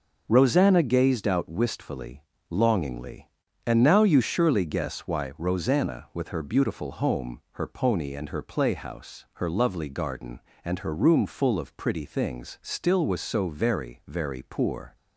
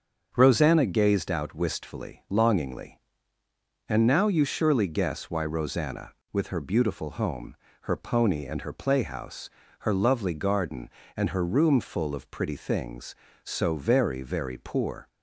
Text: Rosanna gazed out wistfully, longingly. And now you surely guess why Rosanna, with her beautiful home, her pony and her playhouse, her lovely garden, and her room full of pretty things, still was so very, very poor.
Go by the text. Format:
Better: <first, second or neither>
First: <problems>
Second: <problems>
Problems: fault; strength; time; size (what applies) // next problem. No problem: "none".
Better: first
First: none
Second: starts louder than the rest; until 1.3 s; 7 dB // skips "still was"; at 13.2 s